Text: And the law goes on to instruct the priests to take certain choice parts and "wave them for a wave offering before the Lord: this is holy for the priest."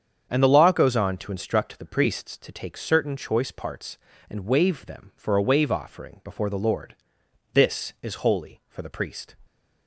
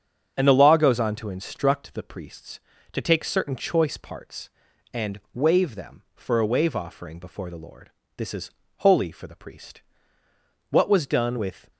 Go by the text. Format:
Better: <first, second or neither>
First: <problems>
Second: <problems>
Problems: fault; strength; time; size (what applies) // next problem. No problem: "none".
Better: first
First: starts louder than the rest; strong; until 1.3 s; 7.5 dB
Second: starts louder than the rest; strong; until 1.3 s; 7.5 dB // pauses between "is" and "holy"; slight; at 8.5 s; 0.26 s long // goes on to say "What was done with"; noticeable; from 10.7 s on; 1.0 s long